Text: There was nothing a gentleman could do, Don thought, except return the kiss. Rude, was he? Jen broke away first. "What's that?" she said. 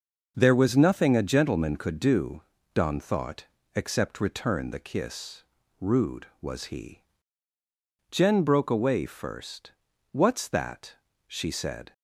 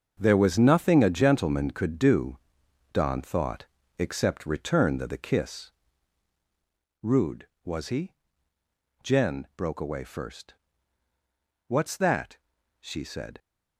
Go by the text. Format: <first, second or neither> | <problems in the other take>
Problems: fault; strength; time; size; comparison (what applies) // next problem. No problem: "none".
first | starts louder than the rest; until 1.2 s; 6.5 dB; noticeable in the first // says "the" twice; at 5.0 s